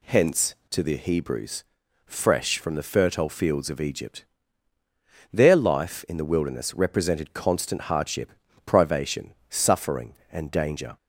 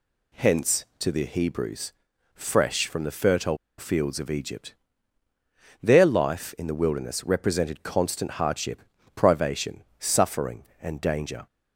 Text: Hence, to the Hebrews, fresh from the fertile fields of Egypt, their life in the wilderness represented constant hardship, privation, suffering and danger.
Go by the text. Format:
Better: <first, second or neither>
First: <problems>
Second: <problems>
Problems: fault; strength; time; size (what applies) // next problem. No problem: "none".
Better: first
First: none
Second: pauses between "fertile" and "fields"; slight; at 3.5 s; 0.21 s long